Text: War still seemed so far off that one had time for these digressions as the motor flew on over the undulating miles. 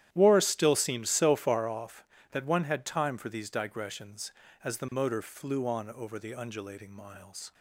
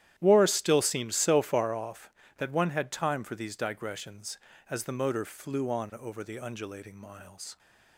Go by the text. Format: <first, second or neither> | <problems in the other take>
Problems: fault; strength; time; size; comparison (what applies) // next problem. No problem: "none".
neither | starts louder than the rest; strong; the same in both